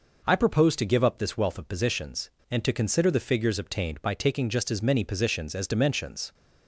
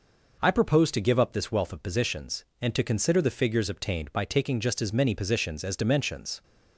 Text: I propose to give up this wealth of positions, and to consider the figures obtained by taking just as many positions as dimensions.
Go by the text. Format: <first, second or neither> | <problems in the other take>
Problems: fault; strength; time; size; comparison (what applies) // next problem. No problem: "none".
neither | none